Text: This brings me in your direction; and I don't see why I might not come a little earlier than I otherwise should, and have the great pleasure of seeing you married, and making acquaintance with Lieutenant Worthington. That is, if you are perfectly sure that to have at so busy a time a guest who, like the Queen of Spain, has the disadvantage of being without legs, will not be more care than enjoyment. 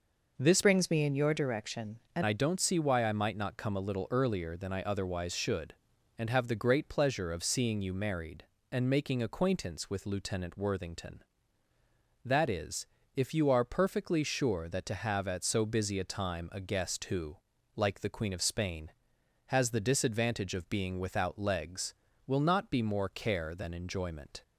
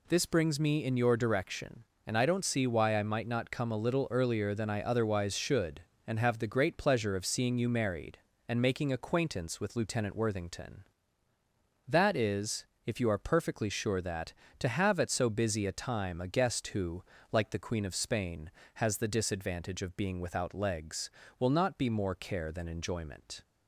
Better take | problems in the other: second | changes voice from "brings" to "and"; from 0.6 to 2.2 s; 1.6 s long

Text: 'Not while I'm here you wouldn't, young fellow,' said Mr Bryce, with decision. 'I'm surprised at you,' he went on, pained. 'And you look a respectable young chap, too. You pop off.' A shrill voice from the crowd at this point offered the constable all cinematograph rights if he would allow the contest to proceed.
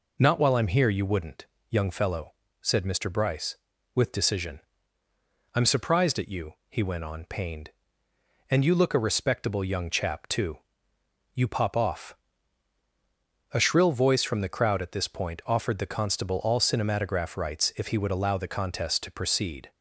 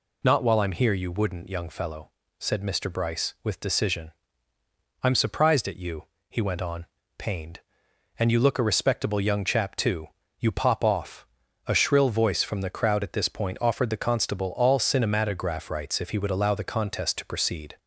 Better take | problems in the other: neither | none

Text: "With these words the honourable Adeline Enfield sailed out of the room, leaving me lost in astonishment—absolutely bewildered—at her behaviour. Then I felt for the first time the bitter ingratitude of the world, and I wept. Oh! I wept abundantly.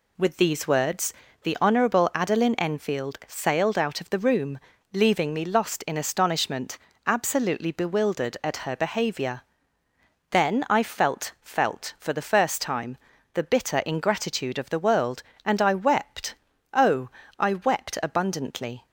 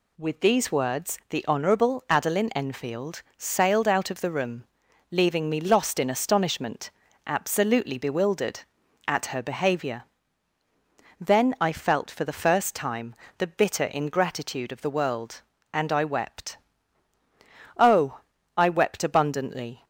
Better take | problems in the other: second | pauses between "words" and "the"; slight; at 1.1 s; 0.32 s long // says "felt" twice; at 11.4 s // pauses between "time" and "the"; at 12.9 s; 0.38 s long; slight in the second

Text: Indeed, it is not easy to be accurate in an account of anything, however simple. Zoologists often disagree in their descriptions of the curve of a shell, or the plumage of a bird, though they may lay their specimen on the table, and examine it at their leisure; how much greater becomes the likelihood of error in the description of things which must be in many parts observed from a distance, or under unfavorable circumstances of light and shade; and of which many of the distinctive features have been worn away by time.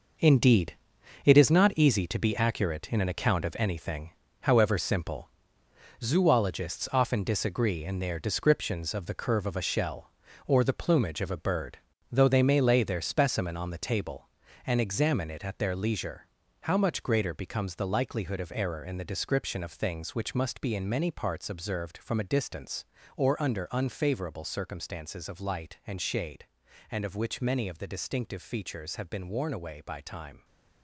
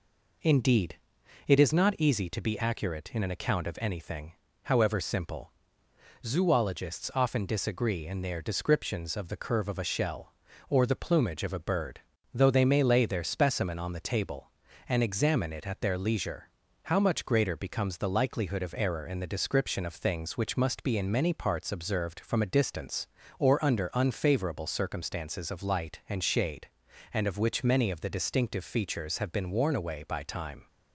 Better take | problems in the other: second | gets quieter; strong; throughout; 8.5 dB

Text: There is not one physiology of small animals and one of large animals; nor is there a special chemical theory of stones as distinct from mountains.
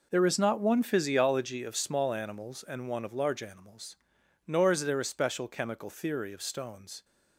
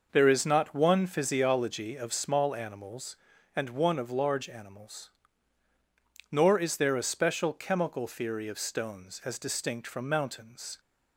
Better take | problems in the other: second | stops before "as distinct from mountains"; at 7.0 s

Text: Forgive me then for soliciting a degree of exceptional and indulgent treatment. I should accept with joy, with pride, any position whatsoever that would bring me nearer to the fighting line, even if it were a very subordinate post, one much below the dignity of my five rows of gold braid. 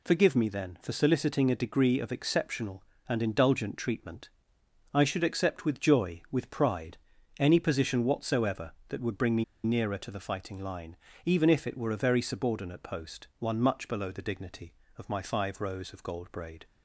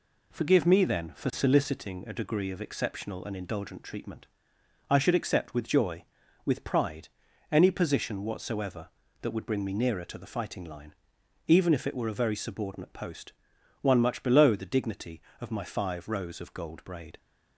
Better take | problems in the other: second | pauses between "me" and "nearer"; slight; at 9.4 s; 0.19 s long

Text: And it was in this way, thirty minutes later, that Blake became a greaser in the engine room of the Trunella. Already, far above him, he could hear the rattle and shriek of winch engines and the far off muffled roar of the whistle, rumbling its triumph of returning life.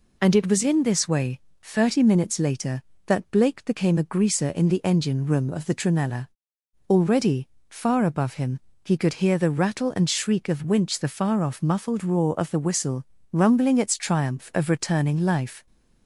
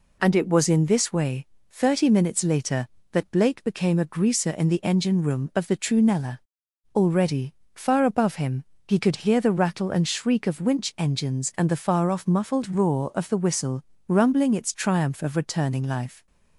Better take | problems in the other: second | skips "engines and"; at 10.9 s

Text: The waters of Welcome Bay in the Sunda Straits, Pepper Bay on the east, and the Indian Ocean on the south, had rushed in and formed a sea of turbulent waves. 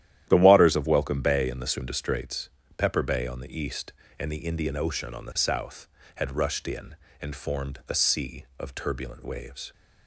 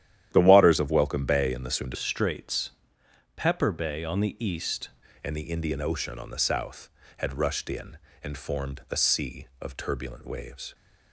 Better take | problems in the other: first | starts louder than the rest; strong; until 1.3 s; 11.5 dB; strong in the first // changes voice from "Straits" to "east"; from 1.9 to 4.8 s; 2.9 s long

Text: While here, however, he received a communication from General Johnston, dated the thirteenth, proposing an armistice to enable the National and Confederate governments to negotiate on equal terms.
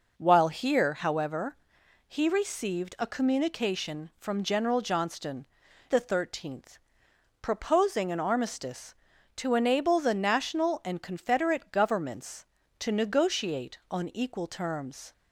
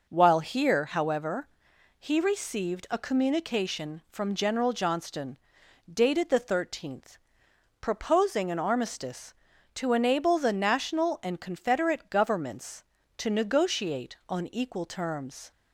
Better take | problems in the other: second | skips "dated"; at 5.6 s

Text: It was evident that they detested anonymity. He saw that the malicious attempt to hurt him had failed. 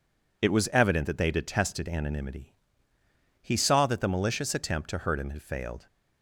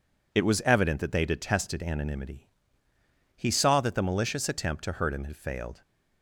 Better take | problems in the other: neither | none

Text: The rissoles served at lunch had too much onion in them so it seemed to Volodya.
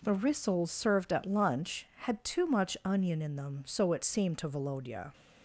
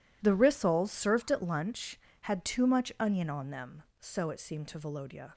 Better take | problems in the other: first | says "on" for "in"; at 3.3 s

